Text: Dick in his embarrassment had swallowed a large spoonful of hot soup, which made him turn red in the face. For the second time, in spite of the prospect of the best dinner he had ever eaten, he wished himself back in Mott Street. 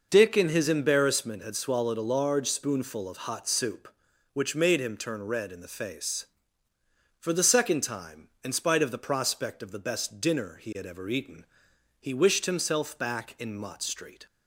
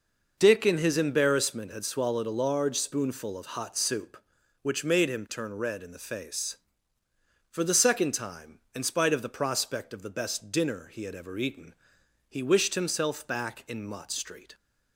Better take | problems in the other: neither | none

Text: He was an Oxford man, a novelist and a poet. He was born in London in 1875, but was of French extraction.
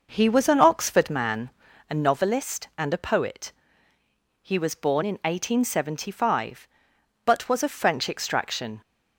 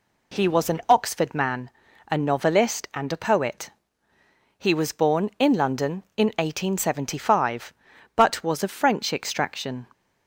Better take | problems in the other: second | skips "in London"; at 5.0 s

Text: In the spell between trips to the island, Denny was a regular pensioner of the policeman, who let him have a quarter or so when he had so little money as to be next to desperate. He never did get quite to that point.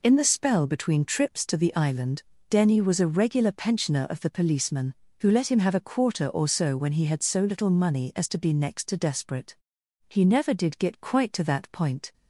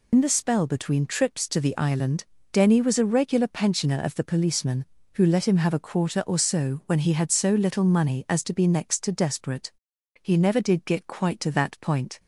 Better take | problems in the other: first | loses the start of "In"; at 0.1 s; 55 ms

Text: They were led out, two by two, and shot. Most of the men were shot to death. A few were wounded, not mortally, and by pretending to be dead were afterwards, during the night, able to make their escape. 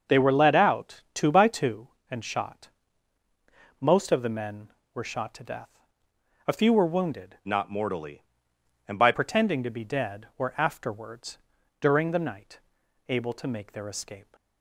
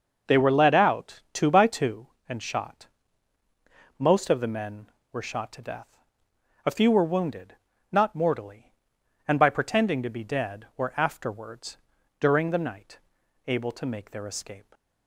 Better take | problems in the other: second | starts louder than the rest; until 1.2 s; 6.5 dB; also in the second // changes voice from "not" to "by"; from 7.4 to 9.1 s; 1.7 s long

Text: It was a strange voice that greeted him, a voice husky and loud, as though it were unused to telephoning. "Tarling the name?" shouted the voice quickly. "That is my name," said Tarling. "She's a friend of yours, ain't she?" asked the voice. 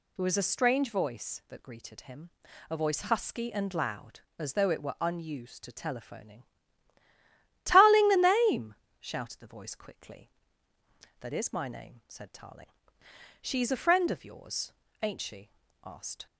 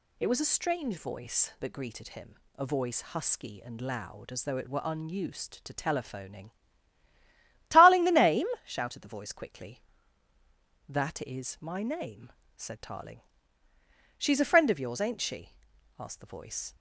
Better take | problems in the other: second | stops before "the voice"; at 16.2 s

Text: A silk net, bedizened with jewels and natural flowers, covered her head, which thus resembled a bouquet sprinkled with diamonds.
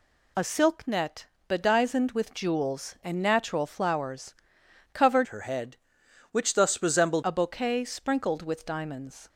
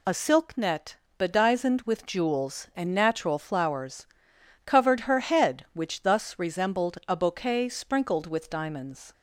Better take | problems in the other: second | changes voice from "her" to "resembled"; from 5.2 to 7.2 s; 2.0 s long

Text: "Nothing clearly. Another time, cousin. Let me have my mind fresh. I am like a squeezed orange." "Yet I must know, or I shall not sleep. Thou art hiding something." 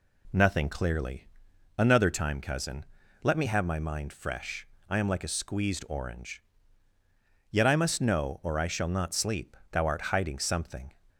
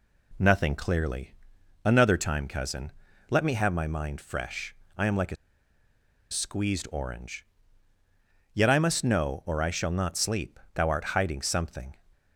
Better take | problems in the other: first | pauses between "a" and "squeezed"; noticeable; at 5.3 s; 0.95 s long

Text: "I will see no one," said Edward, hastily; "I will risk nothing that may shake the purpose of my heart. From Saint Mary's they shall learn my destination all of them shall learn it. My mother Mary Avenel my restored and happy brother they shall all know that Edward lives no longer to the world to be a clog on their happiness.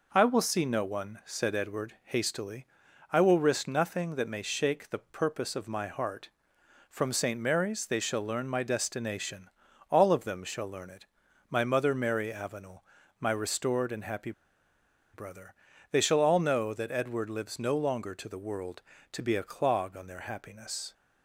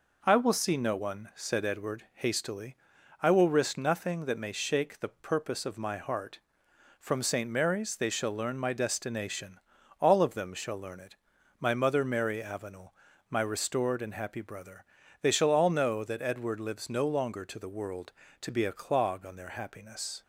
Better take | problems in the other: second | pauses between "destination" and "all"; at 9.4 s; 0.40 s long; also in the second // pauses between "Avenel" and "my"; slight; at 12.8 s; 0.34 s long; slight in the second // pauses between "happy" and "brother"; noticeable; at 14.3 s; 0.82 s long // pauses between "brother" and "they"; slight; at 15.5 s; 0.36 s long; slight in the second

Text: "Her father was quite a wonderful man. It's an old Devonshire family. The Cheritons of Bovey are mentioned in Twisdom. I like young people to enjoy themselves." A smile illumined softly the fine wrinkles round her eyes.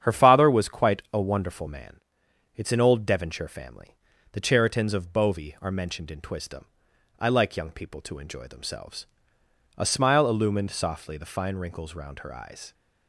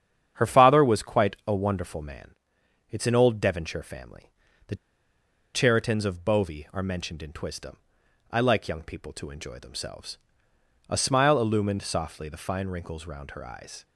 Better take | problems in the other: first | starts louder than the rest; strong; until 1.3 s; 8.5 dB; strong in the first // pauses between "The" and "Cheritons"; noticeable; at 4.7 s; 0.79 s long

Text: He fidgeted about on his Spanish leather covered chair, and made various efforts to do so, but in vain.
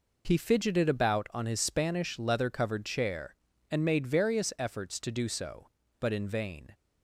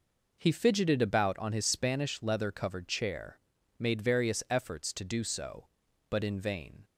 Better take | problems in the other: first | skips "and"; at 3.5 s

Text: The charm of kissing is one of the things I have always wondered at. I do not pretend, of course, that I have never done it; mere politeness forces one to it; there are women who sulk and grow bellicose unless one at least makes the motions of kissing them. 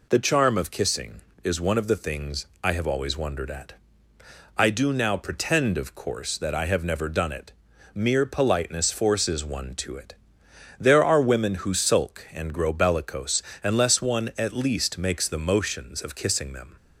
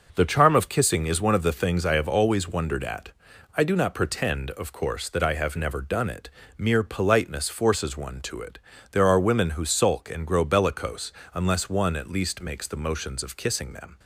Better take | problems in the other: second | pauses between "things" and "I"; slight; at 2.4 s; 0.16 s long // says "now" for "not"; at 4.9 s // pauses between "bellicose" and "unless"; slight; at 13.4 s; 0.22 s long; slight in the second

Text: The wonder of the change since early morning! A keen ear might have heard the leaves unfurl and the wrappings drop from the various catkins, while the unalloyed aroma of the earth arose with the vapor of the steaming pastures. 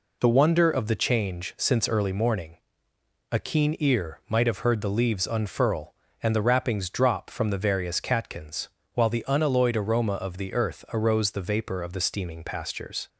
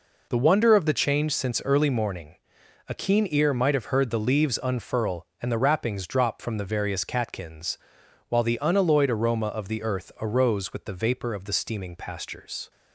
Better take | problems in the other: second | skips "with"; at 11.3 s

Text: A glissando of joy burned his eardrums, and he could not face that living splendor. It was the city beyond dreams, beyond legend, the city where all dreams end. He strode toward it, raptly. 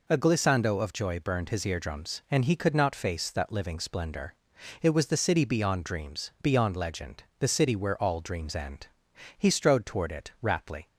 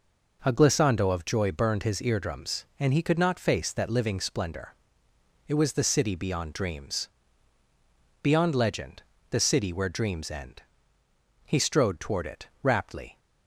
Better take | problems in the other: first | skips "all"; at 9.9 s

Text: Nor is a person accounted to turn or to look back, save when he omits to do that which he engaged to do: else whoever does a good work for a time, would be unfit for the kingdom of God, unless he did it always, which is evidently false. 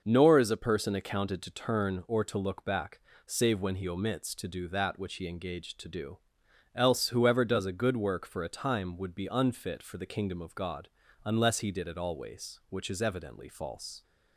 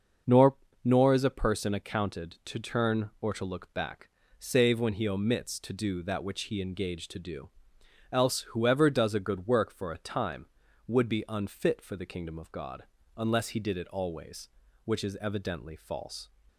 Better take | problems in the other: first | starts louder than the rest; noticeable; until 1.5 s; 6 dB // says "Nor" twice; at 0.8 s

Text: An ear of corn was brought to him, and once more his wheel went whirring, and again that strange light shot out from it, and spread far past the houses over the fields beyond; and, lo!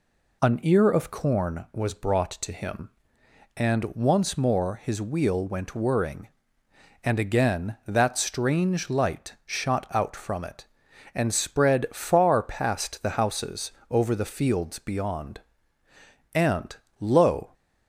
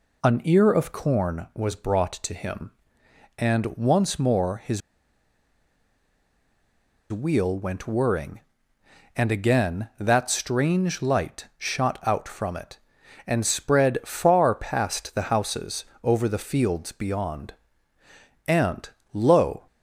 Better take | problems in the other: first | pauses between "his" and "wheel"; strong; at 4.8 s; 2.3 s long // pauses between "houses" and "over"; slight; at 15.8 s; 0.18 s long; slight in the first

